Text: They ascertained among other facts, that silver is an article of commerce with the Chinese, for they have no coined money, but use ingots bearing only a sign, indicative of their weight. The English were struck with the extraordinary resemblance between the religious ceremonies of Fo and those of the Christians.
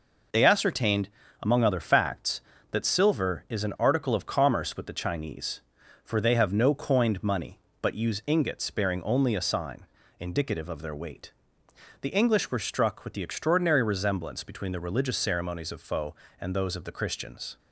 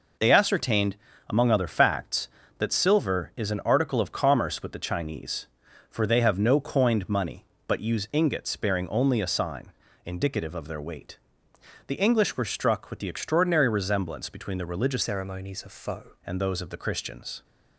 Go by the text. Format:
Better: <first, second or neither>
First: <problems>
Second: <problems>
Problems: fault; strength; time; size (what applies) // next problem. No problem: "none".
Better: first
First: pauses between "ascertained" and "among"; slight; at 1.0 s; 0.32 s long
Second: pauses between "ascertained" and "among"; slight; at 0.9 s; 0.32 s long // changes voice from "ceremonies" to "Fo"; from 15.0 to 16.1 s; 1.1 s long